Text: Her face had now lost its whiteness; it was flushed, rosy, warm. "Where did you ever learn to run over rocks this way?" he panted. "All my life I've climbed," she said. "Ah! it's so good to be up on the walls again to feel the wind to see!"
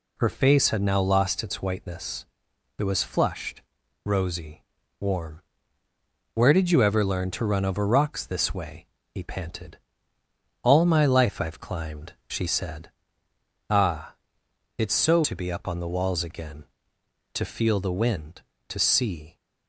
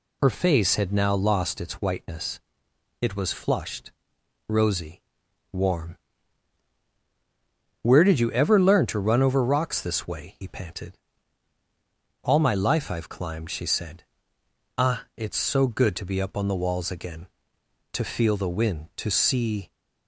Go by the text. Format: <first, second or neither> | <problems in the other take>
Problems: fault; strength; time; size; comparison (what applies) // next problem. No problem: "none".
second | skips "good"; at 15.2 s